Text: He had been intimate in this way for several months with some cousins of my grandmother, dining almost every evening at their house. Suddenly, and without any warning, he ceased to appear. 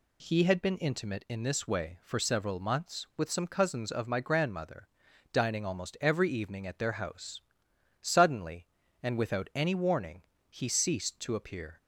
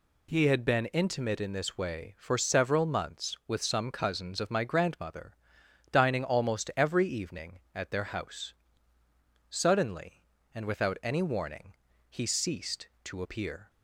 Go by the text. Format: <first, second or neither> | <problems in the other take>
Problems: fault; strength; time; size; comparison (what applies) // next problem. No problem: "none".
neither | none